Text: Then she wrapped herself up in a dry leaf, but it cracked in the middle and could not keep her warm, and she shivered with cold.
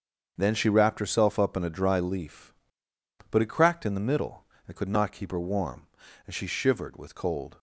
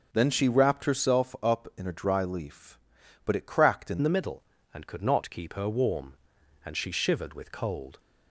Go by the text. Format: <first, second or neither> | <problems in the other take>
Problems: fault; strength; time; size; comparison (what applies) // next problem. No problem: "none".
first | starts louder than the rest; until 1.1 s; 6.5 dB; also in the first // changes voice at "the"; from 4.0 s on; 3.9 s long